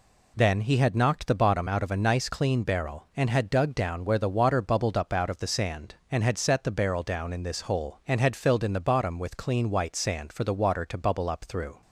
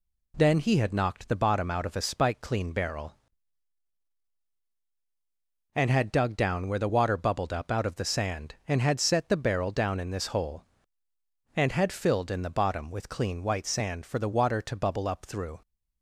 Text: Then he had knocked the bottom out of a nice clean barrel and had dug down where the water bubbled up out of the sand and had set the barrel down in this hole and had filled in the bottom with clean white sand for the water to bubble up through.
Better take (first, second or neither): first